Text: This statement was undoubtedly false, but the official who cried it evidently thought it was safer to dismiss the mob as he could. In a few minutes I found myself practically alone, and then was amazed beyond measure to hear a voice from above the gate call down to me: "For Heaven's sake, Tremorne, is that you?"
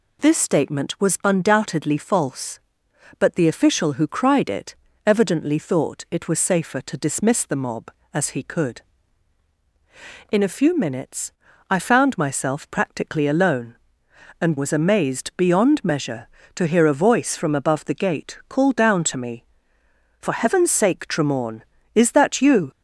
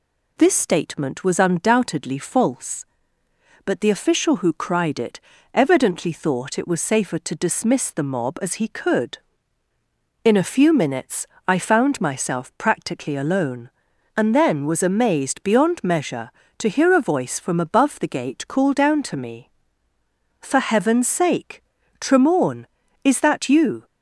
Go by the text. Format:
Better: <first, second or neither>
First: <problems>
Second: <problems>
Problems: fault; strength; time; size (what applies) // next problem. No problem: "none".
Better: second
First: pauses between "it" and "evidently"; slight; at 4.7 s; 0.32 s long // pauses between "minutes" and "I"; at 11.3 s; 0.38 s long // skips "then"; at 14.5 s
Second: pauses between "it" and "evidently"; slight; at 5.1 s; 0.36 s long // pauses between "minutes" and "I"; slight; at 11.2 s; 0.22 s long